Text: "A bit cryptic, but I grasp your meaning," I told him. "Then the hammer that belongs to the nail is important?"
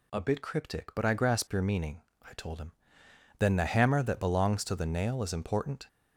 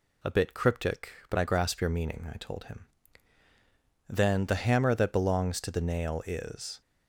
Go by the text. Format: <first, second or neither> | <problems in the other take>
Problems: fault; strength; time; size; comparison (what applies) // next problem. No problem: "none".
first | stops before "important"; at 6.8 s